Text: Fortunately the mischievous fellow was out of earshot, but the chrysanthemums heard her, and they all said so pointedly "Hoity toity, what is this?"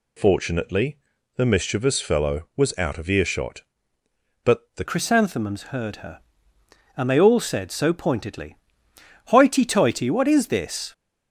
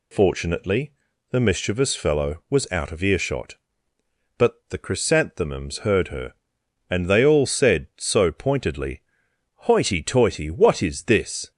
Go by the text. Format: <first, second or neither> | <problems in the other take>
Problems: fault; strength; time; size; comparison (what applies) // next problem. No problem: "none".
second | pauses between "Fortunately" and "the"; at 0.9 s; 0.38 s long; also in the second // changes voice at "chrysanthemums"; from 4.8 s on; 6.1 s long // pauses between "pointedly" and "Hoity"; noticeable; at 8.5 s; 0.70 s long; noticeable in the second